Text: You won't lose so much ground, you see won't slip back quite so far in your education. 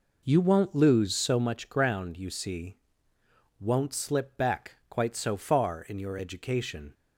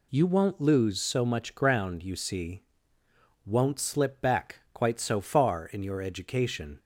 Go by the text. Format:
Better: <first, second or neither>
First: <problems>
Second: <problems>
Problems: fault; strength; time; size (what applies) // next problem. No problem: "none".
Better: second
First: starts louder than the rest; noticeable; until 1.5 s; 4 dB // pauses between "see" and "won't"; noticeable; at 2.7 s; 0.82 s long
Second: pauses between "see" and "won't"; noticeable; at 2.6 s; 0.82 s long